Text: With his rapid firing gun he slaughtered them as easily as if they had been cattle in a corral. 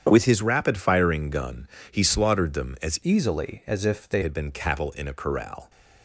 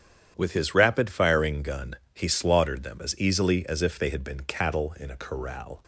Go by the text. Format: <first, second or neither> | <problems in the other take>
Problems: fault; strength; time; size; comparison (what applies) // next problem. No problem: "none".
second | starts louder than the rest; strong; until 1.1 s; 8.5 dB; strong in the second // pauses between "gun" and "he"; slight; at 1.6 s; 0.24 s long; slight in the second // changes voice from "easily" to "they"; from 3.0 to 4.2 s; 1.2 s long